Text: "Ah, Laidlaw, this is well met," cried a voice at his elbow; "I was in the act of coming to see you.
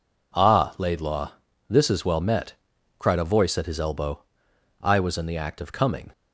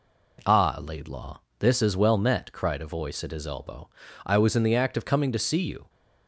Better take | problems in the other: second | stops before "to see you"; at 6.1 s

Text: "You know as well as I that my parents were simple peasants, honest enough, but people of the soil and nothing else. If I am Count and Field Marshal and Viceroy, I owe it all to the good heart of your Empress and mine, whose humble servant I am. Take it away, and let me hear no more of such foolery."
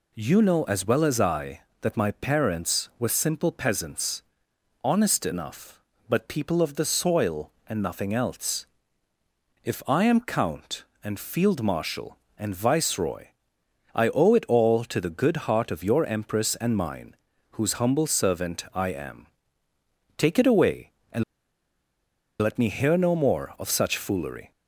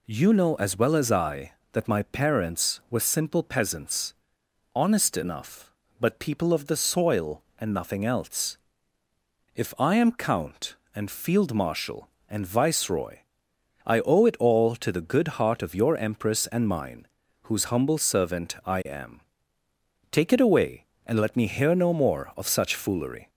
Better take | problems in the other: second | pauses between "and" and "let"; at 21.2 s; 1.1 s long

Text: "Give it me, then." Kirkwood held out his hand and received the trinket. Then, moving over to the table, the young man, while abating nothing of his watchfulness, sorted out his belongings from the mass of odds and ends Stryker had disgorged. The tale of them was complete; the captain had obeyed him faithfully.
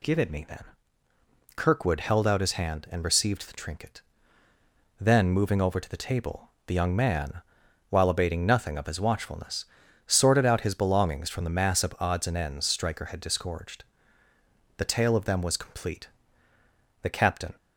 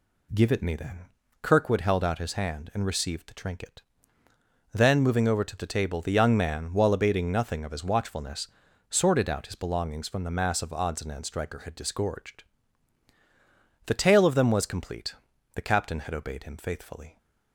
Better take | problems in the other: second | stops before "had obeyed him faithfully"; at 17.5 s

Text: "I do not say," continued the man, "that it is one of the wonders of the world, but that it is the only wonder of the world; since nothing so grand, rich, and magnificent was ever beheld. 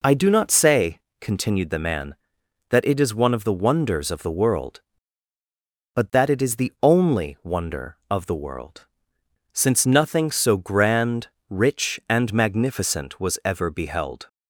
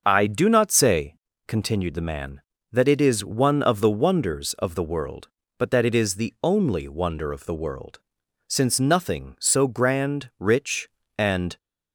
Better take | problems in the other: first | starts louder than the rest; until 1.0 s; 6.5 dB // stops before "magnificent was ever beheld"; at 11.5 s

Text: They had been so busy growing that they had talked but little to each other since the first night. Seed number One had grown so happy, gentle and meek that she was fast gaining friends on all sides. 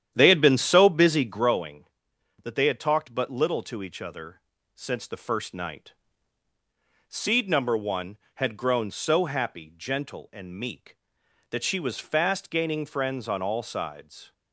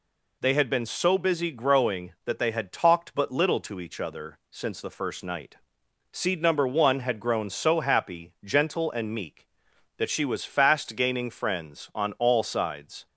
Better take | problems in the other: second | starts louder than the rest; strong; until 1.5 s; 10 dB // pauses between "other" and "since"; slight; at 4.4 s; 0.34 s long

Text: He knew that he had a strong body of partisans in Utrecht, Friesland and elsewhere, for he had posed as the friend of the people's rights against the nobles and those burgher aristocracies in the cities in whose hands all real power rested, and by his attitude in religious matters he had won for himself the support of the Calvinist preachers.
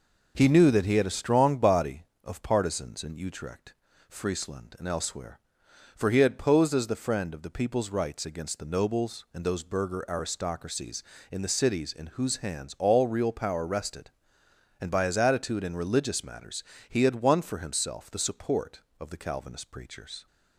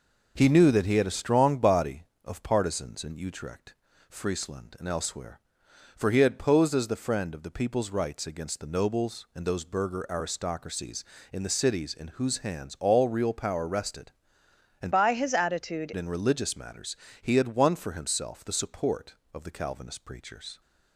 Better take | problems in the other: first | changes voice from "by" to "attitude"; from 14.9 to 15.9 s; 1.0 s long // pauses between "matters" and "he"; slight; at 16.9 s; 0.26 s long; slight in the first

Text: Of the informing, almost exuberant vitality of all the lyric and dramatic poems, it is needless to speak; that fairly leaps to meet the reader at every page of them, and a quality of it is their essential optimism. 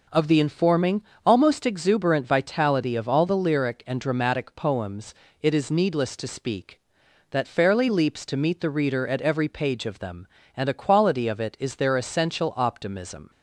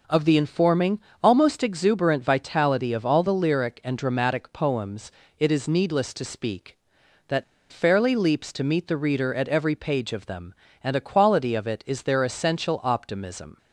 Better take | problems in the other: first | pauses between "that" and "fairly"; slight; at 7.4 s; 0.29 s long

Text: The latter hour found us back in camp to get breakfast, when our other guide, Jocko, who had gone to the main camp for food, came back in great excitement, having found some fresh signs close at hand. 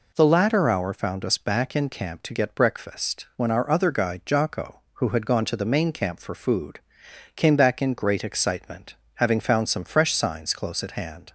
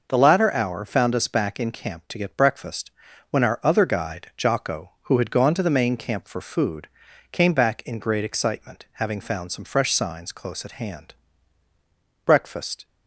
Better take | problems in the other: first | goes on to say "Breakfast"; from 12.2 s on; 0.60 s long

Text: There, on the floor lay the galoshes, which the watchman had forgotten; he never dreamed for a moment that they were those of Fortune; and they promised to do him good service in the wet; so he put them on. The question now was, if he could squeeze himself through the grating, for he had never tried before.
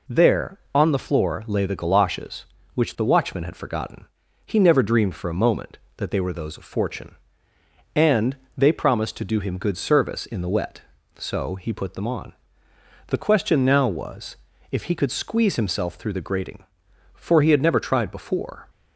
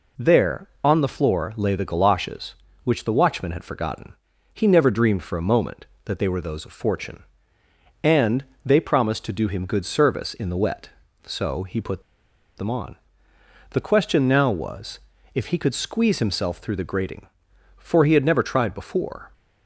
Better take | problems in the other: first | pauses between "and" and "they"; slight; at 8.4 s; 0.18 s long; slight in the first // pauses between "put" and "them"; noticeable; at 11.9 s; 0.57 s long

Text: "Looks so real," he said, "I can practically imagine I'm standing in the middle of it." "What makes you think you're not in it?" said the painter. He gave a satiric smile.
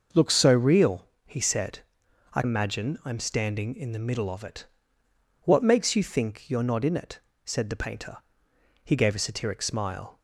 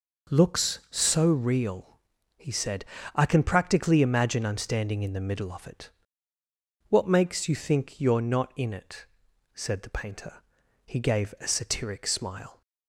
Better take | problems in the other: second | starts louder than the rest; noticeable; until 1.3 s; 6 dB // skips "can practically"; at 2.4 s

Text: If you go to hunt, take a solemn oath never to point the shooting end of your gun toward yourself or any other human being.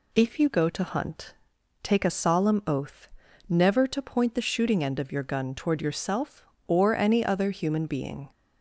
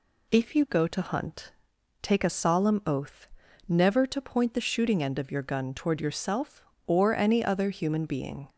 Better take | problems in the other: neither | pauses between "oath" and "never"; the same in both

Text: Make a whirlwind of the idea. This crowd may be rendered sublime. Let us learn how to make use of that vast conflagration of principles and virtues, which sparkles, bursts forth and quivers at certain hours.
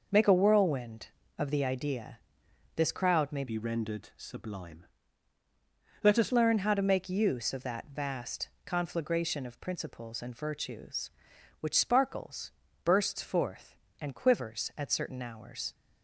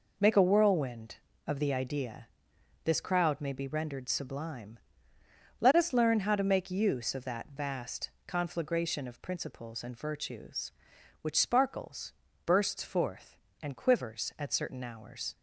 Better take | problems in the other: second | changes voice from "be" to "us"; from 3.4 to 6.3 s; 2.9 s long // pauses between "vast" and "conflagration"; slight; at 8.4 s; 0.16 s long; slight in the second

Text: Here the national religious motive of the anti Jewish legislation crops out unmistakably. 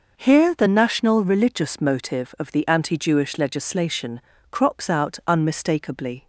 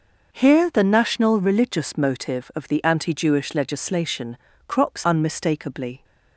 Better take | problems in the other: first | pauses between "legislation" and "crops"; slight; at 4.3 s; 0.30 s long; slight in the first // skips "out"; at 5.0 s

